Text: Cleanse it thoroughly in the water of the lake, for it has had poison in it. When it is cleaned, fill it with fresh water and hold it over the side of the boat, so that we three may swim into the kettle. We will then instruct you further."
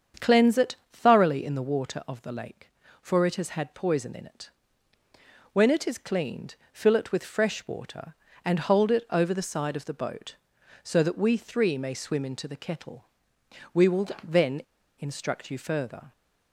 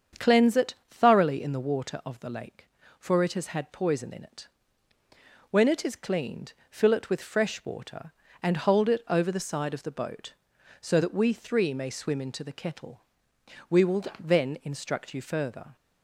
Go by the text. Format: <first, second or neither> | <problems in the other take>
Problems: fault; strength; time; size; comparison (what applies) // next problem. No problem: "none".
second | starts louder than the rest; strong; until 1.3 s; 7.5 dB; strong in the second // pauses between "it" and "thoroughly"; slight; at 0.7 s; 0.16 s long // pauses between "then" and "instruct"; at 14.6 s; 0.38 s long